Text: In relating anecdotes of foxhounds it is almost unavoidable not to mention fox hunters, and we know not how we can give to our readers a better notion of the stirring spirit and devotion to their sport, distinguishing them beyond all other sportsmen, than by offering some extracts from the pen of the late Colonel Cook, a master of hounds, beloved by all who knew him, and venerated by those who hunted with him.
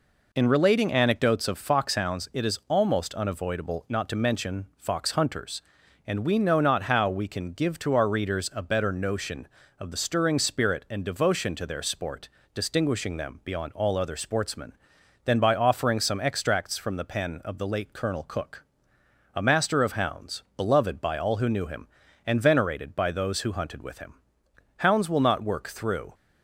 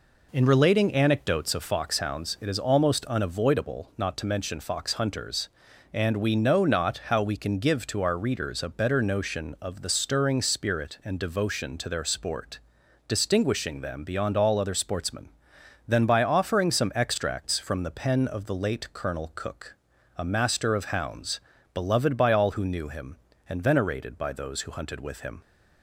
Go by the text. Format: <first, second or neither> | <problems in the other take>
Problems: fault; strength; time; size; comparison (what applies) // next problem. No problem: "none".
second | goes on to say "Hounds will not work through"; from 24.7 s on; 1.3 s long